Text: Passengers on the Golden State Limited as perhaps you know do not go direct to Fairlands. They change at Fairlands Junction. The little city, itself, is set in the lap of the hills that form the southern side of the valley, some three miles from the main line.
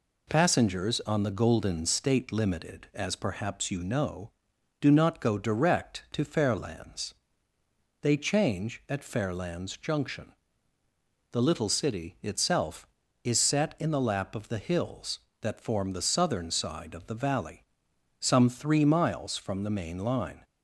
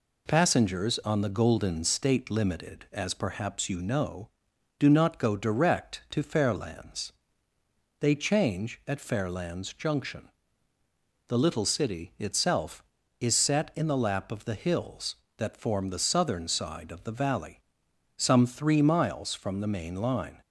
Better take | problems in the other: neither | none

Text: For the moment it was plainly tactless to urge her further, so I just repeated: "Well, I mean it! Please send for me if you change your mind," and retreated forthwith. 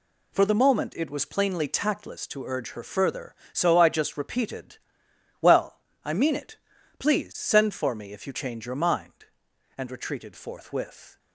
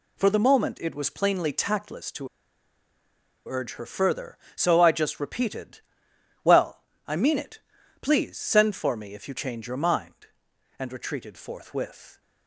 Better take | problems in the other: first | pauses between "to" and "urge"; at 2.2 s; 1.2 s long

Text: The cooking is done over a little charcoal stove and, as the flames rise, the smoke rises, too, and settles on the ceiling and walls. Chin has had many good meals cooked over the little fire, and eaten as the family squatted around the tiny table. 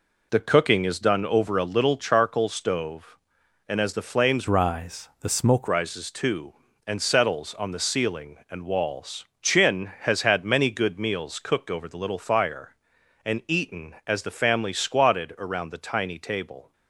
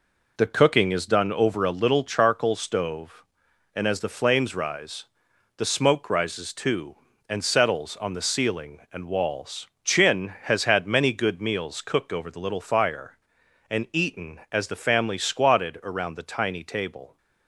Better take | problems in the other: second | changes voice from "rise" to "smoke"; from 4.4 to 5.6 s; 1.2 s long

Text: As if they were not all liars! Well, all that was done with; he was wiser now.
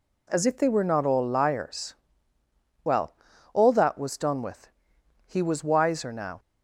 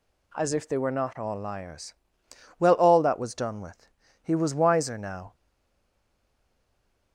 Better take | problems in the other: first | stays silent after the last word; noticeable; from 5.3 s on; 1.8 s long

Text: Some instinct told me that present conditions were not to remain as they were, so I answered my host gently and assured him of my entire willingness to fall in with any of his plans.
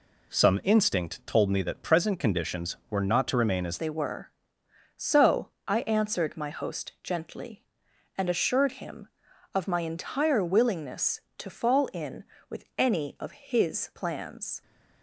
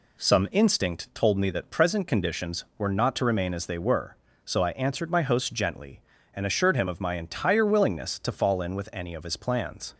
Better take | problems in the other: second | changes voice at "they"; from 3.7 s on; 10.9 s long // pauses between "so" and "I"; slight; at 5.4 s; 0.16 s long

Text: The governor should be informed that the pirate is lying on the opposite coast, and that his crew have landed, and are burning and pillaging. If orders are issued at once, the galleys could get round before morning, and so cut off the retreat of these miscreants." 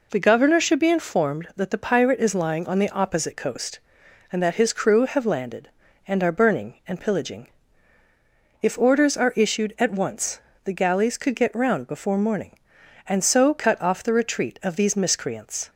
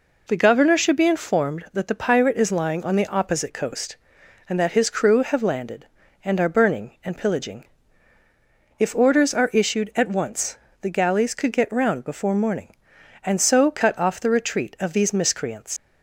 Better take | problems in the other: first | leaves "miscreants" unfinished; at 15.7 s; 100 ms

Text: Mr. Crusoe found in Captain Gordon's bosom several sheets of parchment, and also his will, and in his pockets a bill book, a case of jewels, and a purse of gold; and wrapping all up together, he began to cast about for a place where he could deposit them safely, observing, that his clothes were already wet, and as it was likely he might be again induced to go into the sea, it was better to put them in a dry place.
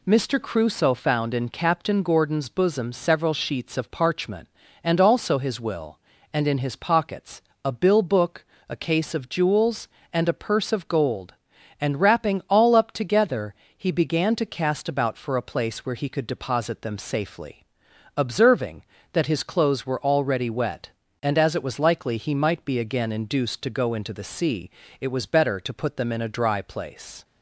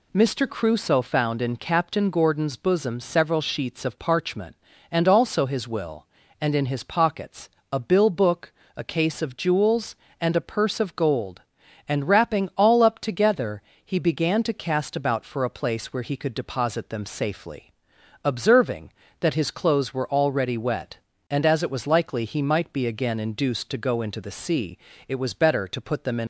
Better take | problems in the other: first | pauses between "pockets" and "a"; slight; at 7.4 s; 0.24 s long; slight in the first // stops before "a dry place"; at 26.2 s

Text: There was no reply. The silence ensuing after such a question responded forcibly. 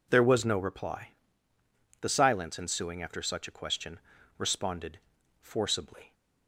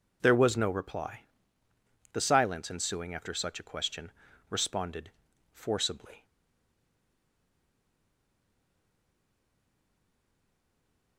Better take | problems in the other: first | pauses between "question" and "responded"; at 4.1 s; 0.40 s long; also in the first // pauses between "responded" and "forcibly"; at 5.0 s; 0.42 s long; also in the first // stays silent after the last word; strong; from 6.2 s on; 4.9 s long

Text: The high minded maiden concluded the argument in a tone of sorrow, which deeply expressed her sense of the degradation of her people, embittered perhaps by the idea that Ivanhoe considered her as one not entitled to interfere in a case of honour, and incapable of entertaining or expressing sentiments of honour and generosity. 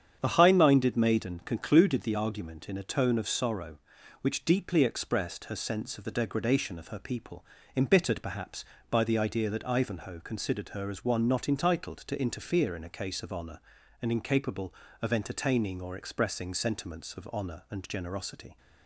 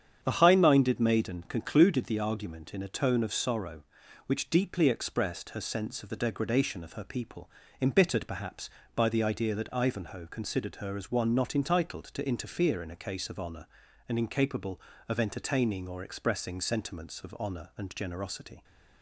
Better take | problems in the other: neither | starts louder than the rest; strong; the same in both

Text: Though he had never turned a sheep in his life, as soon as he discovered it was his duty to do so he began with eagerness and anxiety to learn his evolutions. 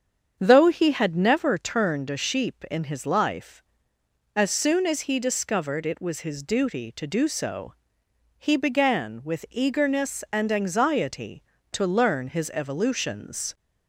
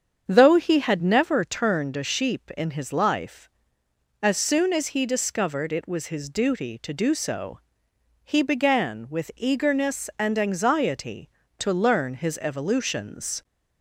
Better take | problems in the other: neither | starts louder than the rest; strong; the same in both // pauses between "so" and "he"; noticeable; the same in both

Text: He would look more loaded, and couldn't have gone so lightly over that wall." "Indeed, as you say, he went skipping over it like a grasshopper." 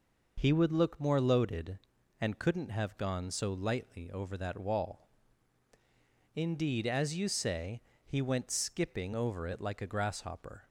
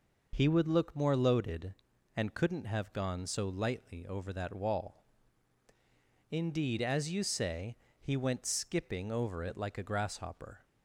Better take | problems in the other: neither | none

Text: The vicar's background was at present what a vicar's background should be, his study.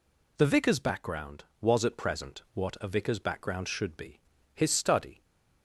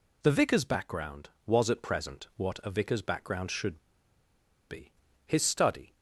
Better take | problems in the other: first | pauses between "should" and "be"; noticeable; at 3.7 s; 0.90 s long

